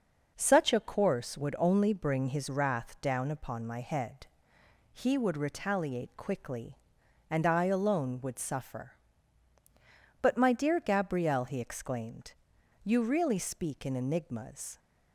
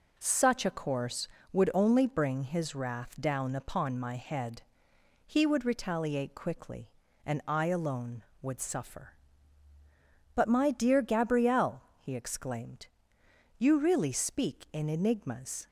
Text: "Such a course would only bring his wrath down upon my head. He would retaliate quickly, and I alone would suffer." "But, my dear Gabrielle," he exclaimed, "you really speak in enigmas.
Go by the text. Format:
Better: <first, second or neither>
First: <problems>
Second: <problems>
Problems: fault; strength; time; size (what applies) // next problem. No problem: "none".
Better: neither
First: none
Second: none